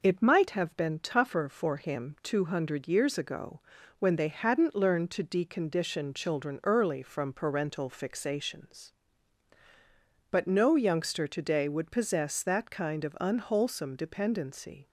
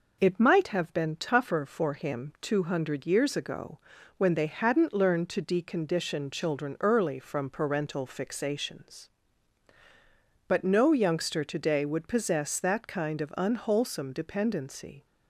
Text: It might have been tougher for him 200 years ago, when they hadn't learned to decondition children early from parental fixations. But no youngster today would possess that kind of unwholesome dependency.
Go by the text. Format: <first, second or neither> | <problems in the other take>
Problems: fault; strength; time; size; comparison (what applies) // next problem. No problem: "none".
neither | none